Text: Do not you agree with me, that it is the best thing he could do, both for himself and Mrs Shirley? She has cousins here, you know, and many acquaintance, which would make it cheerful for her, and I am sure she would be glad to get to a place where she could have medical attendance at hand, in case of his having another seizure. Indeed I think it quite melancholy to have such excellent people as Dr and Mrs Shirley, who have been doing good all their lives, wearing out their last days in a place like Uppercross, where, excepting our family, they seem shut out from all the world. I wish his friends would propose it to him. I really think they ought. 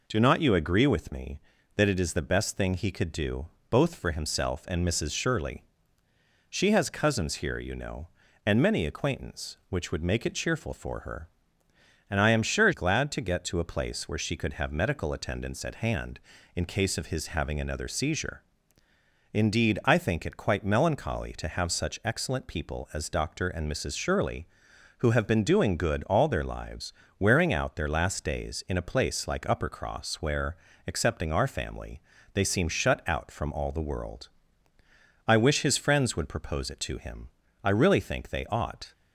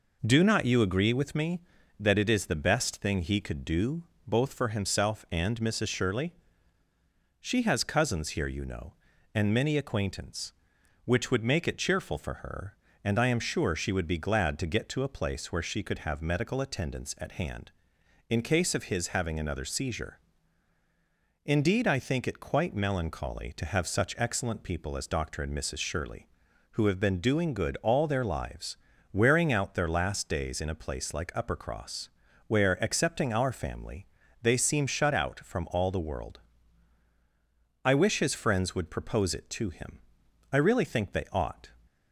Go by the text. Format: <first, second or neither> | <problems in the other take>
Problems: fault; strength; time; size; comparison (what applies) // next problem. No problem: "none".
second | skips "she would be"; at 12.7 s